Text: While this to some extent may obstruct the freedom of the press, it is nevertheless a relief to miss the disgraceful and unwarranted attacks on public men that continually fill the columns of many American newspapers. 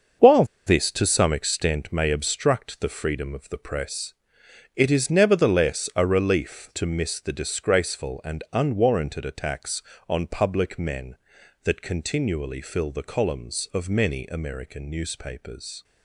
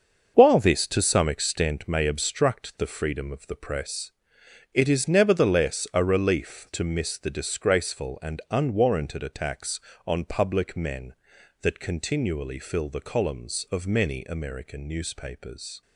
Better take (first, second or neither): second